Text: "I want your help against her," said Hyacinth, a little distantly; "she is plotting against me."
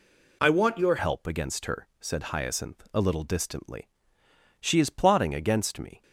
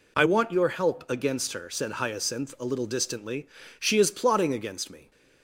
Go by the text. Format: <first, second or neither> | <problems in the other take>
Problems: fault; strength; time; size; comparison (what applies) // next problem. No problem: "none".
second | changes voice at "help"; from 0.9 s on; 5.1 s long